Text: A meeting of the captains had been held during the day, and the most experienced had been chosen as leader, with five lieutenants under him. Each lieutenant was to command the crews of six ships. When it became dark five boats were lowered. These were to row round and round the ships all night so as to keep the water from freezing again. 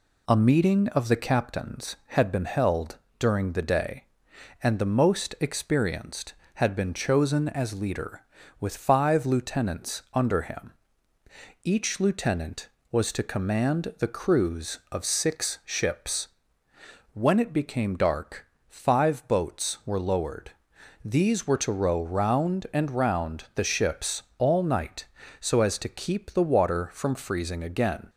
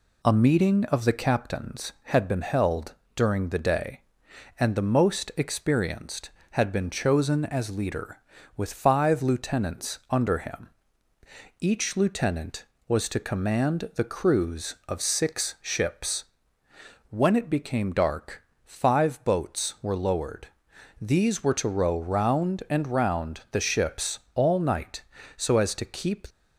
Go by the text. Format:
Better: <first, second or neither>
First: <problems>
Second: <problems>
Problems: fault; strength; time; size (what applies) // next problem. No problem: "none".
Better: first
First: pauses between "held" and "during"; slight; at 2.9 s; 0.22 s long // pauses between "dark" and "five"; slight; at 18.4 s; 0.20 s long // pauses between "ships" and "all"; slight; at 24.2 s; 0.16 s long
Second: pauses between "held" and "during"; slight; at 2.9 s; 0.22 s long // pauses between "dark" and "five"; slight; at 18.4 s; 0.20 s long // pauses between "ships" and "all"; slight; at 24.1 s; 0.16 s long // stops before "the water from freezing again"; at 26.2 s